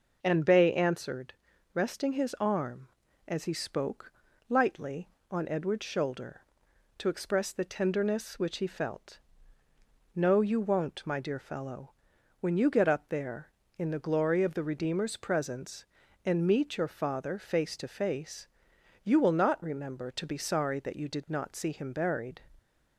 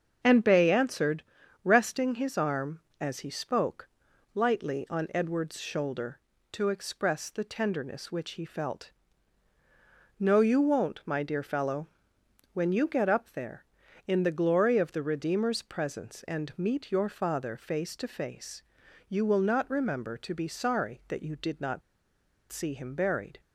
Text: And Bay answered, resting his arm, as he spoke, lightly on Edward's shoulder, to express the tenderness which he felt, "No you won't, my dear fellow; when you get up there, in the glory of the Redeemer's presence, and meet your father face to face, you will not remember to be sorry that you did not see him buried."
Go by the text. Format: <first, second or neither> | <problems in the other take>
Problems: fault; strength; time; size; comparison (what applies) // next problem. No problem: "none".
first | starts louder than the rest; until 1.6 s; 6.5 dB // pauses between "not" and "see"; noticeable; at 21.8 s; 0.70 s long